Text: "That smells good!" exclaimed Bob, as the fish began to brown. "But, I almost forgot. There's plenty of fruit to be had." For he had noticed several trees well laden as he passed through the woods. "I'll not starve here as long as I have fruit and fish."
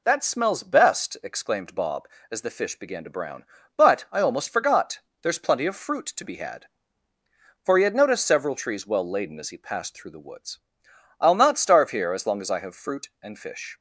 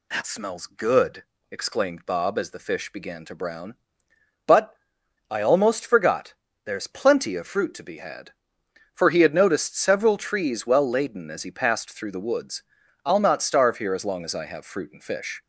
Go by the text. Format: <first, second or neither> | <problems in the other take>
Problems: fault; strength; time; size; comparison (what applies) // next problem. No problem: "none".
second | says "best" for "good"; at 0.6 s